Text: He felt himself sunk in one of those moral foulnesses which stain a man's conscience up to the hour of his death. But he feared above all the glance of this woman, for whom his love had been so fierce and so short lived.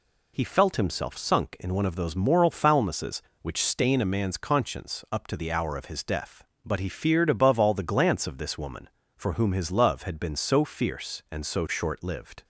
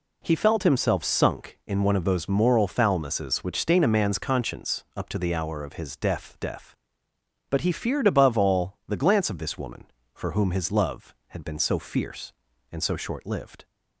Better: first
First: none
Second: says "death" twice; at 6.4 s

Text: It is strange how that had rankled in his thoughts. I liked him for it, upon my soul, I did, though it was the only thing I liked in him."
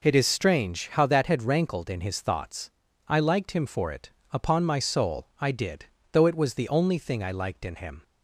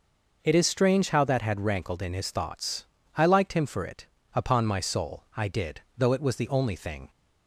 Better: first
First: none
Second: stops before "I liked in him"; at 7.0 s

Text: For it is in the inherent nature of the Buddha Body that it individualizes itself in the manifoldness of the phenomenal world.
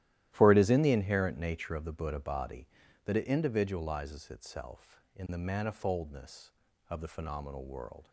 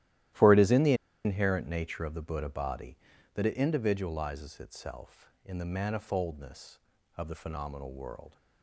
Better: first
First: starts louder than the rest; strong; until 1.3 s; 13.5 dB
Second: starts louder than the rest; strong; until 1.6 s; 13.5 dB // pauses between "the" and "inherent"; slight; at 0.9 s; 0.30 s long

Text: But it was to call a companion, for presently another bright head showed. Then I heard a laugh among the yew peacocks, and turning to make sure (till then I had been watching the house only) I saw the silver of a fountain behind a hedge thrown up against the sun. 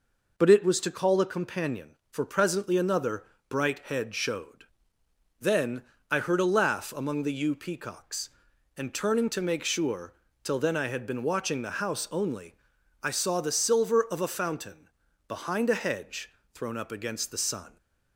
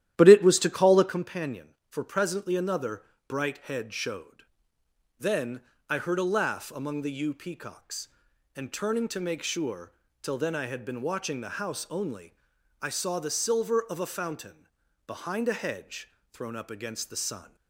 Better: first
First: pauses between "another" and "bright"; slight; at 3.2 s; 0.24 s long // pauses between "Then" and "I"; slight; at 5.8 s; 0.28 s long // pauses between "fountain" and "behind"; at 14.8 s; 0.40 s long // pauses between "hedge" and "thrown"; slight; at 16.3 s; 0.20 s long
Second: starts louder than the rest; strong; until 1.3 s; 12 dB // pauses between "another" and "bright"; slight; at 3.0 s; 0.24 s long // pauses between "Then" and "I"; slight; at 5.6 s; 0.28 s long // pauses between "fountain" and "behind"; at 14.6 s; 0.40 s long // pauses between "hedge" and "thrown"; slight; at 16.1 s; 0.20 s long

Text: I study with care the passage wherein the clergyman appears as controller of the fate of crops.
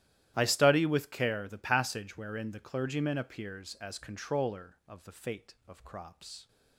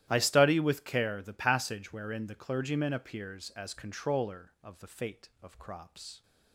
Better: neither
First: starts louder than the rest; strong; until 1.3 s; 13 dB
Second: starts louder than the rest; strong; until 1.1 s; 13 dB

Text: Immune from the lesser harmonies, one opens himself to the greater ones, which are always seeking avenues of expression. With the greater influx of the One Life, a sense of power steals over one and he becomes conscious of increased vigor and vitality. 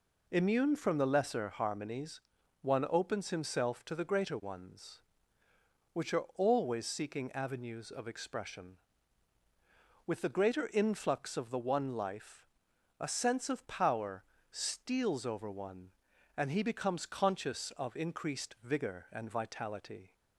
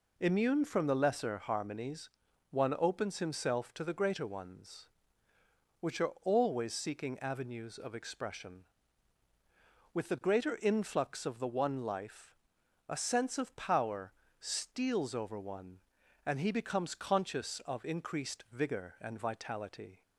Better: neither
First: pauses between "power" and "steals"; slight; at 14.2 s; 0.28 s long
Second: pauses between "power" and "steals"; slight; at 14.1 s; 0.28 s long

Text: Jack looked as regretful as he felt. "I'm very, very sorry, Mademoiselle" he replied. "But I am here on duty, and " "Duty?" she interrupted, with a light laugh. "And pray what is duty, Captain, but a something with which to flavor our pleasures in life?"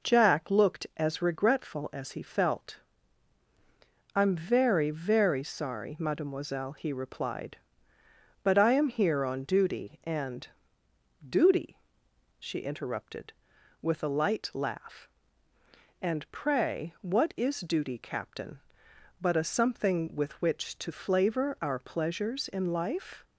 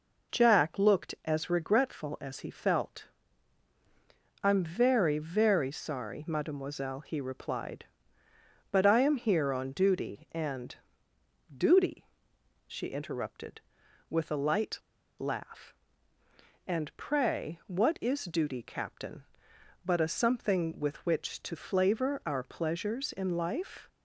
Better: first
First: none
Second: pauses between "light" and "laugh"; at 14.7 s; 0.40 s long

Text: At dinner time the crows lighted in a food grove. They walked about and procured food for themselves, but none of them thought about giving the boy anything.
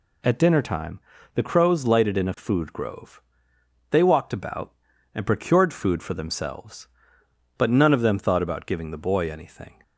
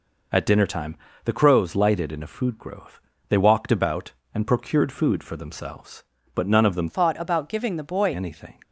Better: first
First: pauses between "time" and "the"; slight; at 0.9 s; 0.36 s long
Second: pauses between "time" and "the"; slight; at 0.9 s; 0.26 s long // changes voice from "thought" to "boy"; from 6.8 to 8.1 s; 1.3 s long

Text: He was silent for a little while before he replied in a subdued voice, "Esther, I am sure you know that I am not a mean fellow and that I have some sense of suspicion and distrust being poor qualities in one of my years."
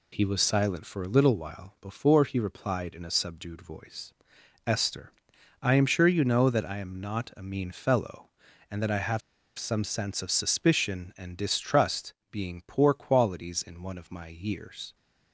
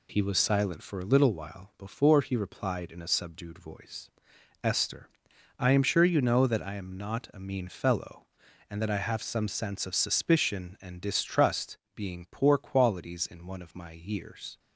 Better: second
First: pauses between "have" and "some"; at 9.2 s; 0.37 s long // pauses between "distrust" and "being"; slight; at 12.1 s; 0.16 s long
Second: pauses between "distrust" and "being"; slight; at 11.7 s; 0.16 s long

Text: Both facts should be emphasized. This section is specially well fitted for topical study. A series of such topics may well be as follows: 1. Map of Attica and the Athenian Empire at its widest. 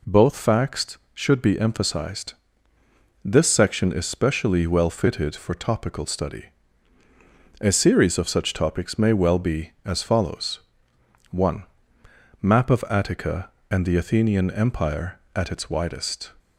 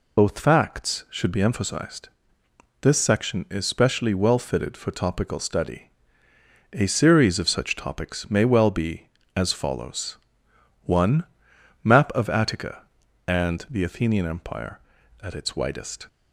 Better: first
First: none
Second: loses the start of "Both"; at 0.1 s; 50 ms

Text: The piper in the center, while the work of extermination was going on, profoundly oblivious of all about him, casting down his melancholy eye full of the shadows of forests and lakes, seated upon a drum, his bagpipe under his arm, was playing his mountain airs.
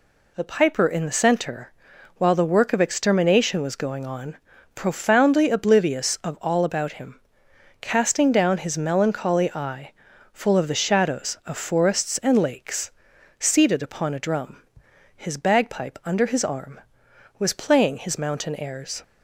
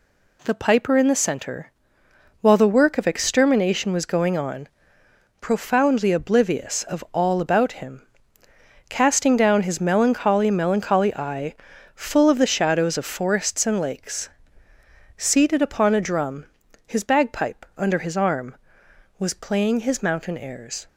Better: first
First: pauses between "eye" and "full"; at 9.9 s; 0.40 s long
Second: says "melancholy" twice; at 10.4 s // pauses between "eye" and "full"; at 11.5 s; 0.38 s long

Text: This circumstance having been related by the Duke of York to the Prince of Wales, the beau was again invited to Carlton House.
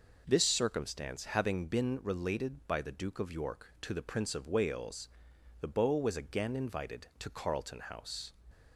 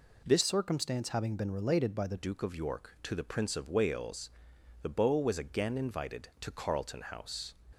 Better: first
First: none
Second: changes voice from "circumstance" to "the"; from 0.4 to 2.1 s; 1.7 s long

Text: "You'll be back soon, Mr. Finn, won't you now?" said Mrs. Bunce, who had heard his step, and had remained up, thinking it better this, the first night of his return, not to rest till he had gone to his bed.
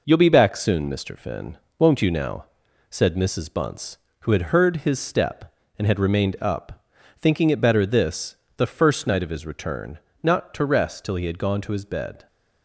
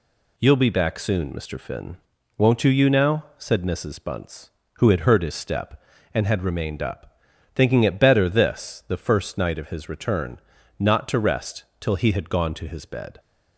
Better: first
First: none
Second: says "you" twice; at 2.6 s // pauses between "rest" and "till"; slight; at 11.6 s; 0.16 s long

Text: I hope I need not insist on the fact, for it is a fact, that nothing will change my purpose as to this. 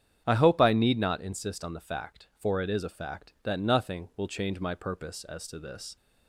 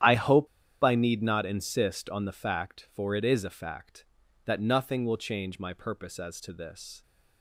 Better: first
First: starts louder than the rest; strong; until 1.2 s; 8.5 dB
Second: starts louder than the rest; strong; until 1.4 s; 10.5 dB // pauses between "hope" and "I"; at 0.4 s; 0.36 s long

